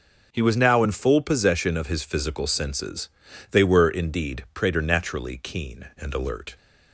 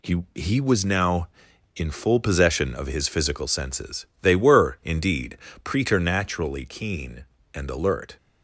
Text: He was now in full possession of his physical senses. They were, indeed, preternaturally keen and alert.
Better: first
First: none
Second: says "He" twice; at 0.3 s

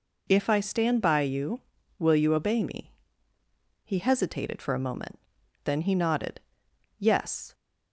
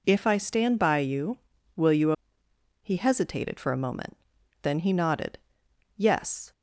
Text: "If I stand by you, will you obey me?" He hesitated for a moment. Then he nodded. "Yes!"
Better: first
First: none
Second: skips "obey me"; at 2.4 s

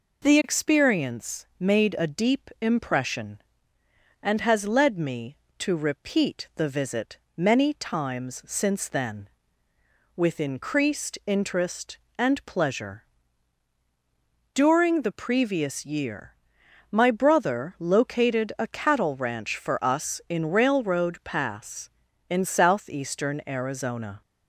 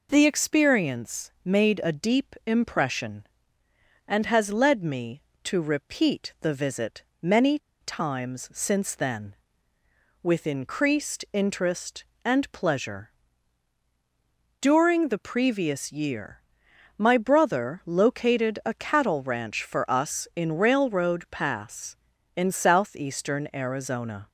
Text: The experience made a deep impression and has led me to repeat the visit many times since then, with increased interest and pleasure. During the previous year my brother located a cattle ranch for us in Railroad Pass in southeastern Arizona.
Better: first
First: pauses between "visit" and "many"; slight; at 7.1 s; 0.18 s long // pauses between "year" and "my"; noticeable; at 16.3 s; 0.56 s long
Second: pauses between "visit" and "many"; slight; at 7.0 s; 0.18 s long // pauses between "many" and "times"; slight; at 7.5 s; 0.22 s long // pauses between "year" and "my"; noticeable; at 16.3 s; 0.56 s long

